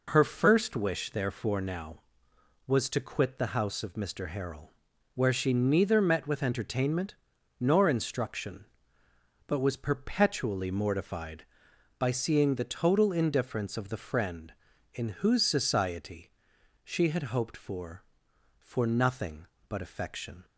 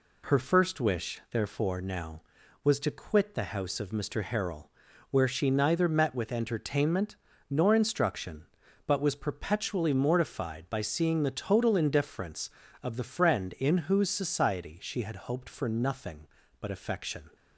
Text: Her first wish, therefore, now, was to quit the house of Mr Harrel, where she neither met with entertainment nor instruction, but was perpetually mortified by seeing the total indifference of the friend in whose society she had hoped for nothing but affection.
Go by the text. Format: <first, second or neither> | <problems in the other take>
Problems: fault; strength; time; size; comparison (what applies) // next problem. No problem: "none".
second | pauses between "entertainment" and "nor"; noticeable; at 7.1 s; 0.48 s long; slight in the second // pauses between "society" and "she"; noticeable; at 16.3 s; 0.52 s long // says "for" twice; at 18.6 s